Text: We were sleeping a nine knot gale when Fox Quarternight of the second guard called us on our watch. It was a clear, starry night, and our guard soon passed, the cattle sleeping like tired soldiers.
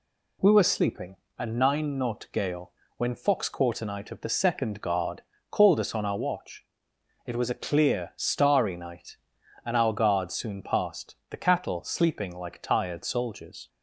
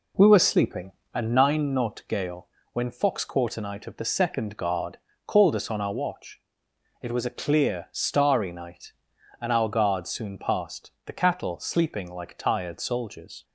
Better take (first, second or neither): first